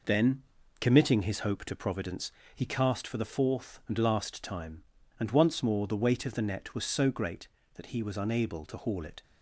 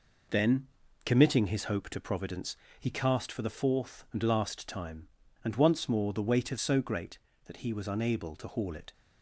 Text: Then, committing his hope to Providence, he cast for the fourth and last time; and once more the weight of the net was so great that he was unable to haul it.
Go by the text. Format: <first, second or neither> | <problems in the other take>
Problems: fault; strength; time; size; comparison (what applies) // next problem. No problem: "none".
first | skips "the net was"; at 6.5 s